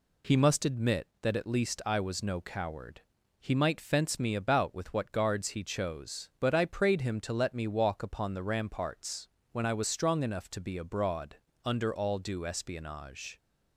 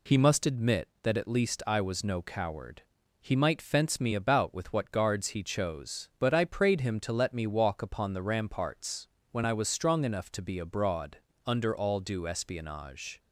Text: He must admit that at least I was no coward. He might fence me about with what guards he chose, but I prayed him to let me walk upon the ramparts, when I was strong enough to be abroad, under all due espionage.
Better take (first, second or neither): neither